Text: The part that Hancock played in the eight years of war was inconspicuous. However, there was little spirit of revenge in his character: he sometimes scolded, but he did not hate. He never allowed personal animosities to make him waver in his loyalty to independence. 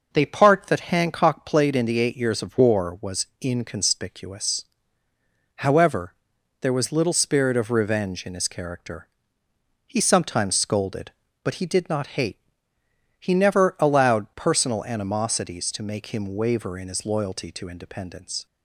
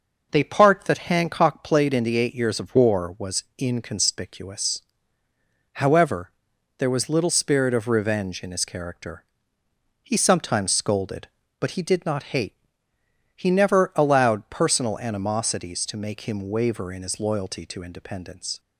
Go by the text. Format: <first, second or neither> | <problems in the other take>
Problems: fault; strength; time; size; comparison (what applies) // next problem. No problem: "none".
neither | none